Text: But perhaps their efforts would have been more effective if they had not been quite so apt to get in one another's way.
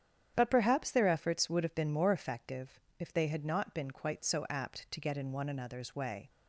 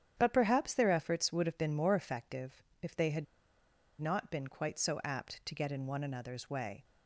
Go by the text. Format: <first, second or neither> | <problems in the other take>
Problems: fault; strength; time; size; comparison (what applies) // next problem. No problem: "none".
first | starts louder than the rest; strong; until 1.1 s; 9.5 dB; strong in the first // pauses between "effective" and "if"; slight; at 2.6 s; 0.20 s long; slight in the first // pauses between "had" and "not"; noticeable; at 3.2 s; 0.76 s long